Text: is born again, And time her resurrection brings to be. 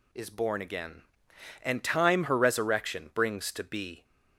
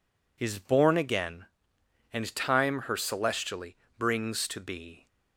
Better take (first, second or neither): first